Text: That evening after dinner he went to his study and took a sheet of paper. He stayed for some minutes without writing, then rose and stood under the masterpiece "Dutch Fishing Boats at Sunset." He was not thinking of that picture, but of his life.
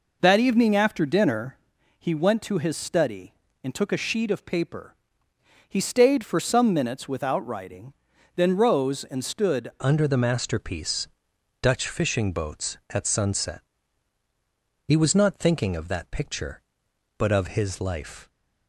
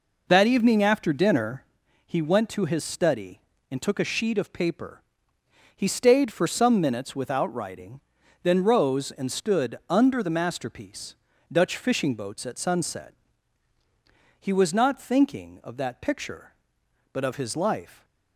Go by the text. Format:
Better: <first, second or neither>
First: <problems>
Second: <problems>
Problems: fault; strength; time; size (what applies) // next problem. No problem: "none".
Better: second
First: pauses between "dinner" and "he"; at 1.5 s; 0.42 s long // changes voice at "under"; from 9.8 s on; 8.4 s long // pauses between "masterpiece" and "Dutch"; noticeable; at 11.0 s; 0.52 s long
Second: pauses between "dinner" and "he"; at 1.6 s; 0.42 s long // pauses between "masterpiece" and "Dutch"; at 11.1 s; 0.38 s long